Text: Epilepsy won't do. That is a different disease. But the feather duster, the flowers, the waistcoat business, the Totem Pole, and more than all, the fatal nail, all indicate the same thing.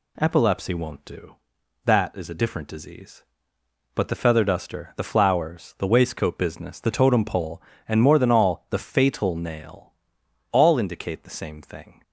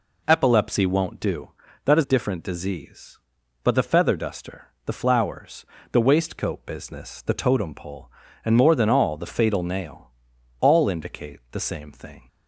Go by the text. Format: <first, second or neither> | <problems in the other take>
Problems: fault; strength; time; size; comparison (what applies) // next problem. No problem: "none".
first | skips "a"; at 2.0 s